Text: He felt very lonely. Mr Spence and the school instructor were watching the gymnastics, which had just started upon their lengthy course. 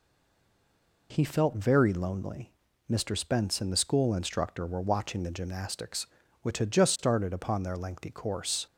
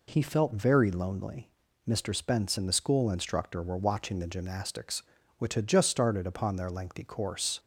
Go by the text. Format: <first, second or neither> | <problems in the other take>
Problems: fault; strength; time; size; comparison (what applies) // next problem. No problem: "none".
second | stays silent before the first word; until 1.1 s; 1.1 s long